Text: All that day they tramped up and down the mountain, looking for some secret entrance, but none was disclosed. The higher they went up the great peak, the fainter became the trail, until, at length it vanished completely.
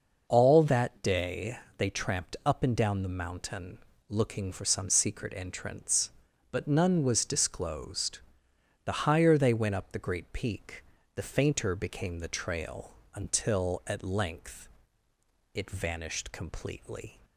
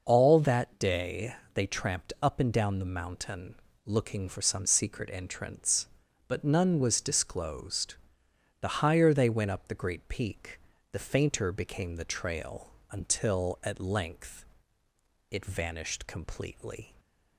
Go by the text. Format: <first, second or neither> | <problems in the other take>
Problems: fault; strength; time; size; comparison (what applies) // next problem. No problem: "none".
neither | pauses between "day" and "they"; slight; the same in both // pauses between "length" and "it"; noticeable; the same in both